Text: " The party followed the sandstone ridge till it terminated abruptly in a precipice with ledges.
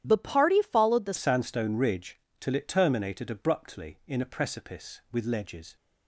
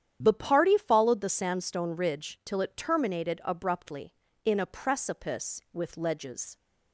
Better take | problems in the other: second | starts louder than the rest; strong; until 1.0 s; 11 dB; strong in the second // changes voice at "sandstone"; from 1.1 s on; 4.6 s long // pauses between "ridge" and "till"; slight; at 2.1 s; 0.22 s long

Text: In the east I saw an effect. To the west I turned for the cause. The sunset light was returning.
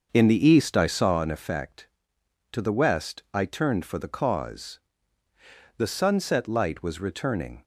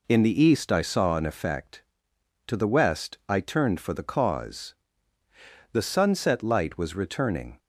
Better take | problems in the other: second | starts louder than the rest; noticeable; until 1.3 s; 6 dB

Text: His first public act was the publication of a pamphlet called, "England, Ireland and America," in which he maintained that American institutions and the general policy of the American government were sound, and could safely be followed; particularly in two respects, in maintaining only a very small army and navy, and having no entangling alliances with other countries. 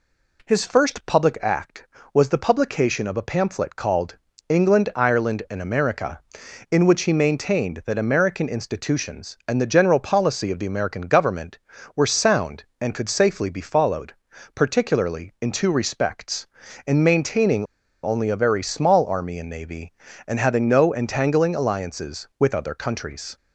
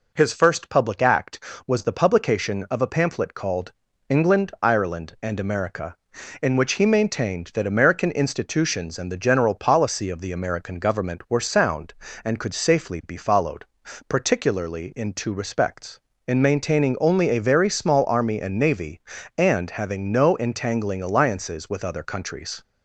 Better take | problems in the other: second | pauses between "maintaining" and "only"; at 17.6 s; 0.38 s long

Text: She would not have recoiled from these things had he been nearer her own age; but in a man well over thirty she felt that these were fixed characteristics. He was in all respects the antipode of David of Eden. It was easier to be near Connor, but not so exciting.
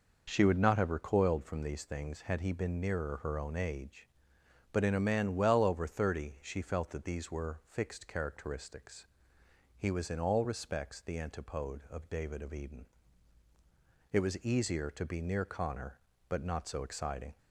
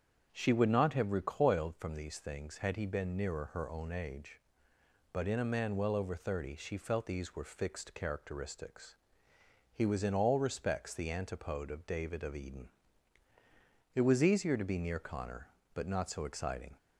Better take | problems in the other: first | starts louder than the rest; strong; until 1.3 s; 8 dB // skips "that"; at 7.0 s

